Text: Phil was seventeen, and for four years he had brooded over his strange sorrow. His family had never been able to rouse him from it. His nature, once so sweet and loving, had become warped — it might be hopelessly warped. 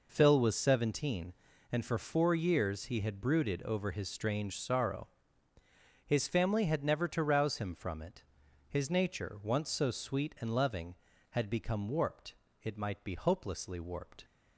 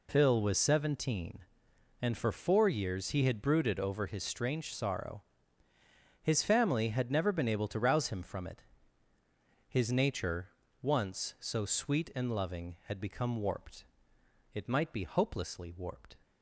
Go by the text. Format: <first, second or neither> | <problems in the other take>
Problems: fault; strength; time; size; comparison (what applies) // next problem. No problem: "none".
second | skips "been able"; at 7.0 s